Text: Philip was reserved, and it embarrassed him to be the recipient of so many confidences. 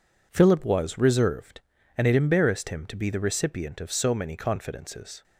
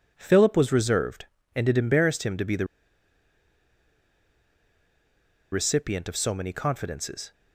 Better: first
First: none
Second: pauses between "the" and "recipient"; strong; at 2.6 s; 2.8 s long

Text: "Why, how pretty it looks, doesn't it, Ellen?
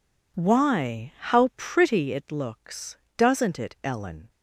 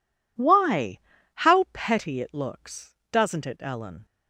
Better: first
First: none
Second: says "petty" for "pretty"; at 1.7 s

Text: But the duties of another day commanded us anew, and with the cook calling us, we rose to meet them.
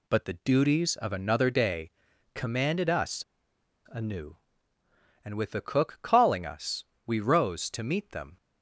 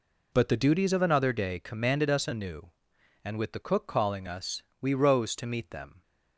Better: second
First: pauses between "day" and "commanded"; at 1.9 s; 0.42 s long // pauses between "us" and "anew"; noticeable; at 3.2 s; 0.64 s long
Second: none

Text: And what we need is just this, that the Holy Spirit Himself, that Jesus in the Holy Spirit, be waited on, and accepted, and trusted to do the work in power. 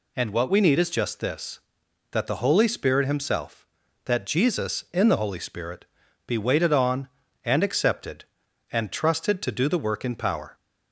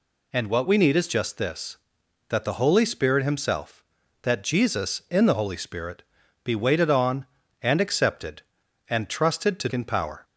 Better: first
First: none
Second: skips "do the work"; at 9.7 s

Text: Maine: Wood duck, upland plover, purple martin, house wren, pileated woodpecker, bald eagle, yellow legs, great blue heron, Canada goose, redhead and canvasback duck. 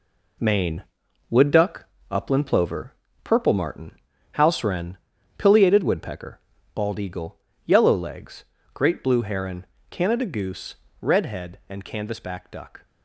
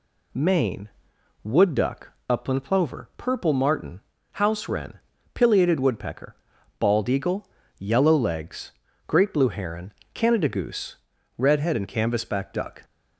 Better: second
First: gets quieter; strong; throughout; 7.5 dB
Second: none

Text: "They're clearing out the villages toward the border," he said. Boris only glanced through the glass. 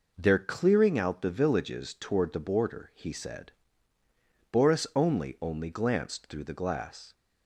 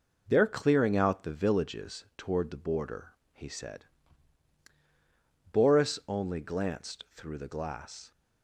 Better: second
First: says "only" twice; at 5.4 s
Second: none

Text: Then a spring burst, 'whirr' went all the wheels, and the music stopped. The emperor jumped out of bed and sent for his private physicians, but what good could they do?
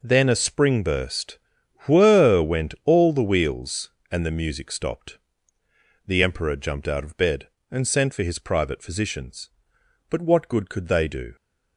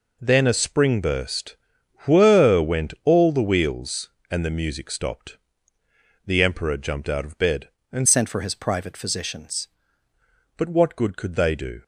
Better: first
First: none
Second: changes voice from "sent" to "physicians"; from 8.0 to 9.6 s; 1.6 s long

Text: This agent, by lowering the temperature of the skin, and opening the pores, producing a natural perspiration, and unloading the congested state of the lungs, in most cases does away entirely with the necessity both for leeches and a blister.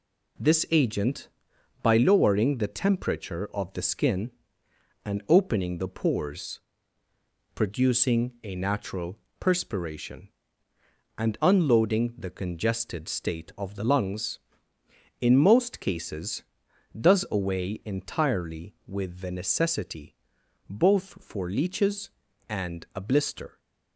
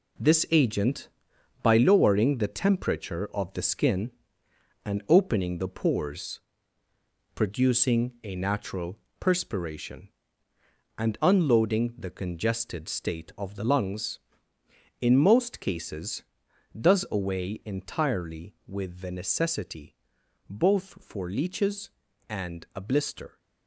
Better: first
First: pauses between "natural" and "perspiration"; slight; at 9.1 s; 0.22 s long // pauses between "necessity" and "both"; noticeable; at 20.1 s; 0.54 s long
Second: gets quieter; strong; throughout; 8 dB // pauses between "natural" and "perspiration"; slight; at 8.9 s; 0.22 s long // pauses between "necessity" and "both"; noticeable; at 19.9 s; 0.54 s long

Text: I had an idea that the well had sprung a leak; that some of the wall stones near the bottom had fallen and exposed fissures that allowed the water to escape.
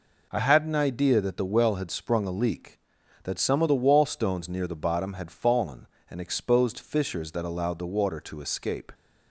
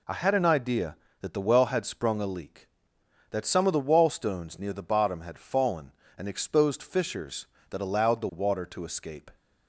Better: neither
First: none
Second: none

